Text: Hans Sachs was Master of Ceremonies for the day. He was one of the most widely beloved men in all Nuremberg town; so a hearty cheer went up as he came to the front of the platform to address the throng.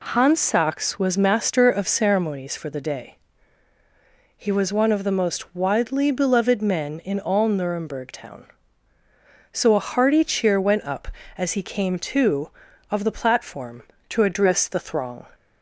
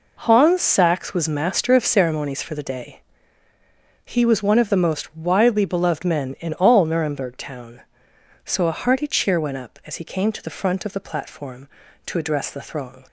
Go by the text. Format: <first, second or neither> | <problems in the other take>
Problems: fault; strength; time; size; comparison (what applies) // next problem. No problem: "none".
second | skips "the front"; at 12.7 s